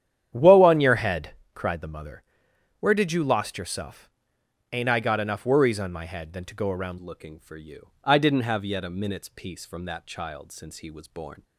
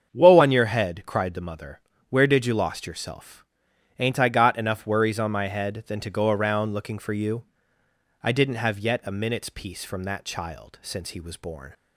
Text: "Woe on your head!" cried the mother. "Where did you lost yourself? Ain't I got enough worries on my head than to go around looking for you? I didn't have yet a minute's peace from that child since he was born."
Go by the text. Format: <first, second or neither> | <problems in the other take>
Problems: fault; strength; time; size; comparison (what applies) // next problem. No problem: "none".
second | starts louder than the rest; strong; until 1.3 s; 10 dB; strong in the second // changes voice at "looking"; from 6.9 s on; 4.5 s long